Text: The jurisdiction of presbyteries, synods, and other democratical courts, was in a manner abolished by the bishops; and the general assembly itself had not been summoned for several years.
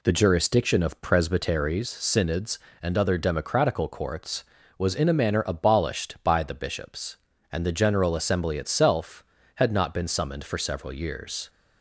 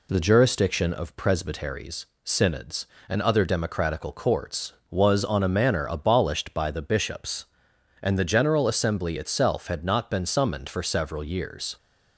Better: first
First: none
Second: says "on" for "in"; at 5.2 s

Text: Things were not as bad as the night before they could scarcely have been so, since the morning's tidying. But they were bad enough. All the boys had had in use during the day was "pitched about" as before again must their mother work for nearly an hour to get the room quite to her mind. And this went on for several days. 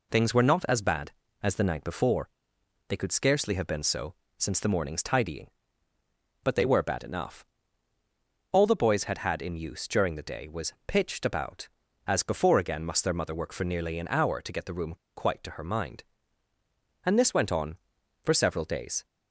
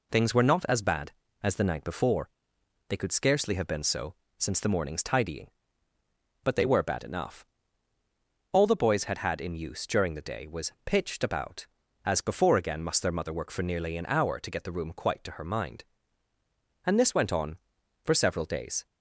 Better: second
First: pauses between "before" and "they"; noticeable; at 2.2 s; 0.60 s long // pauses between "room" and "quite"; slight; at 14.9 s; 0.20 s long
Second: pauses between "before" and "they"; noticeable; at 2.2 s; 0.60 s long

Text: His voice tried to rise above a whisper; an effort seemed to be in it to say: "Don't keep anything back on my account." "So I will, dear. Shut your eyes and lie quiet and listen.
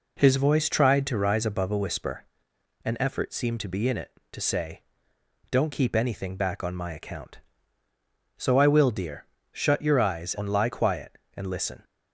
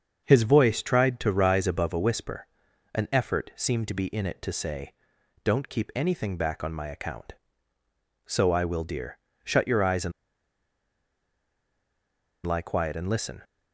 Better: first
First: none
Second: starts louder than the rest; until 1.2 s; 6.5 dB // pauses between "and" and "lie"; strong; at 10.1 s; 2.3 s long

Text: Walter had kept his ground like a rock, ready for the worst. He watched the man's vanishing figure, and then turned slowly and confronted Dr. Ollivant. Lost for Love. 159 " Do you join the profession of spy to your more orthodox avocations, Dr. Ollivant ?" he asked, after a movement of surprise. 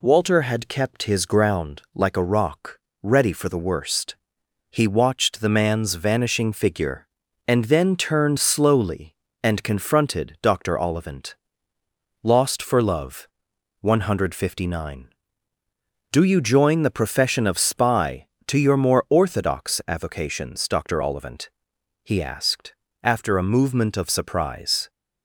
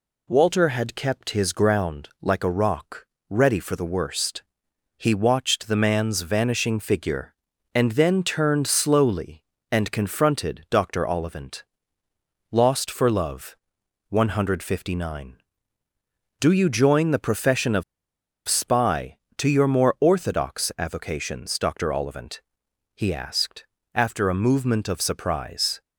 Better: first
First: none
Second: pauses between "of" and "spy"; noticeable; at 17.8 s; 0.65 s long

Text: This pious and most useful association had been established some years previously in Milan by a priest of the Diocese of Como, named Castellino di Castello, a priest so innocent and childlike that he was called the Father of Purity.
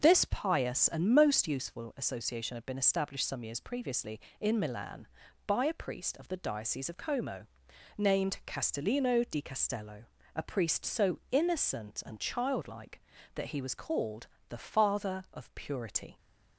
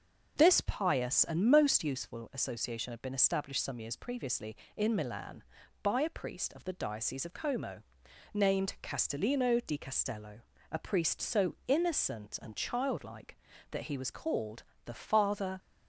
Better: first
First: pauses between "called" and "the"; slight; at 14.2 s; 0.24 s long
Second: pauses between "called" and "the"; slight; at 14.6 s; 0.24 s long // stops before "of Purity"; at 15.5 s

